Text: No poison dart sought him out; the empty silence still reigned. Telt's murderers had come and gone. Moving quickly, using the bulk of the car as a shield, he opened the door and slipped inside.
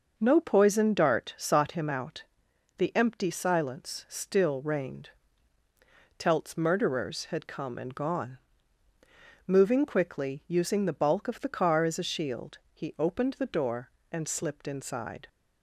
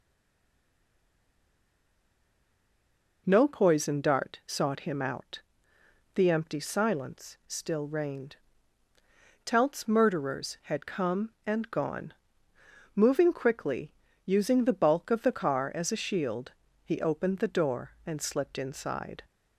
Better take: first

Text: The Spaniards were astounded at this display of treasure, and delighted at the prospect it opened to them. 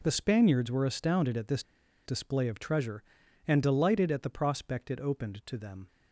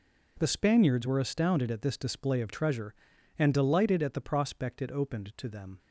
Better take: second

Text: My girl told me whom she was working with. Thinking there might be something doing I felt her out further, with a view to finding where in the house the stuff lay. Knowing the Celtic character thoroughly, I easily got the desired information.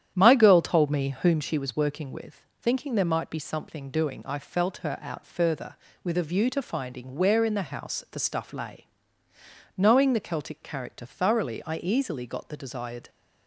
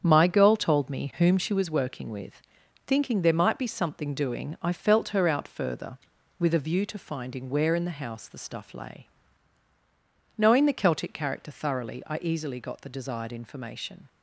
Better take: second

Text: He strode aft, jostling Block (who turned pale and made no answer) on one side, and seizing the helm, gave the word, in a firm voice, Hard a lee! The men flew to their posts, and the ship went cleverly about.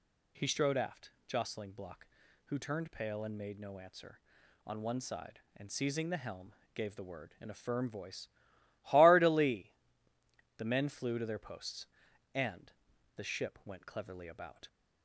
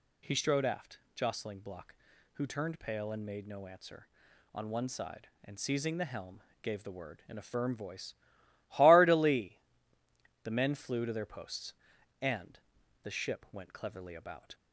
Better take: neither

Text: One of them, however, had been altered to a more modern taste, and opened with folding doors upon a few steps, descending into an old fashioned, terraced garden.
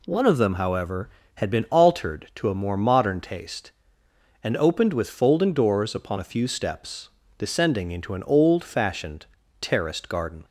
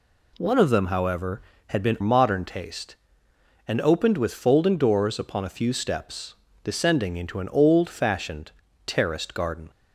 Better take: first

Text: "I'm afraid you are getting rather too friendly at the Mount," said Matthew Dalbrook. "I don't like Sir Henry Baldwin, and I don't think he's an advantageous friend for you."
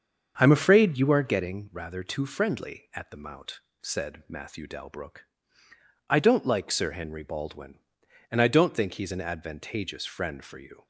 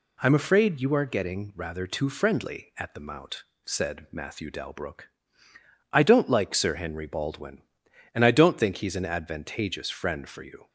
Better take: second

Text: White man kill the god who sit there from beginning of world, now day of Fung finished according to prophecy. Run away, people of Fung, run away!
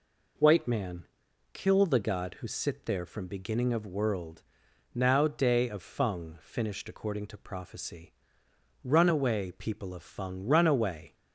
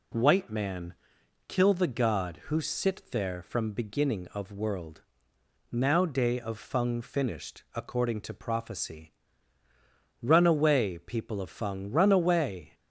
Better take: neither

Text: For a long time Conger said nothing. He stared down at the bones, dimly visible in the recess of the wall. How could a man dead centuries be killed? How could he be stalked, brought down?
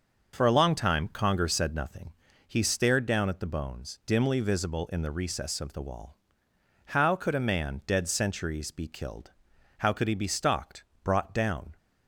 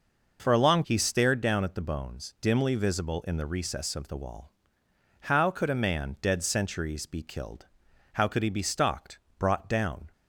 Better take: first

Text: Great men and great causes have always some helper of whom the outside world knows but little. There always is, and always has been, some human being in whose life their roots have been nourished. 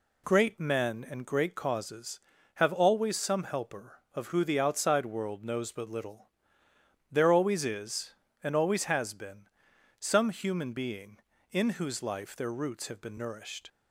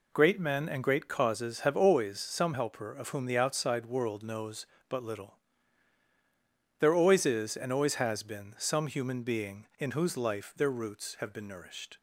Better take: second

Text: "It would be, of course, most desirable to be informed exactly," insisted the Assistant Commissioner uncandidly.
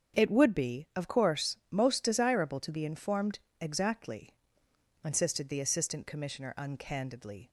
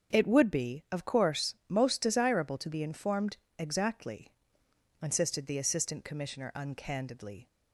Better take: neither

